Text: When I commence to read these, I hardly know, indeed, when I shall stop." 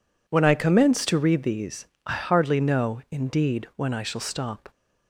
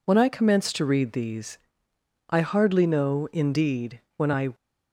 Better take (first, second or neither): first